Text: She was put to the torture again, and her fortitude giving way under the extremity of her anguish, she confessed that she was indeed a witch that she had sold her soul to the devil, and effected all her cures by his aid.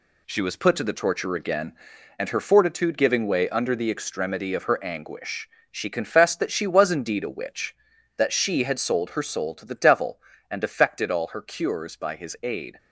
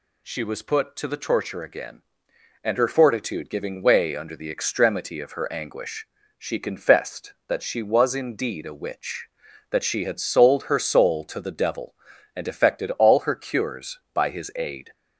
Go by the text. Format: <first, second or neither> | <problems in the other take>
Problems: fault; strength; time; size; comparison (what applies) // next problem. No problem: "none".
neither | none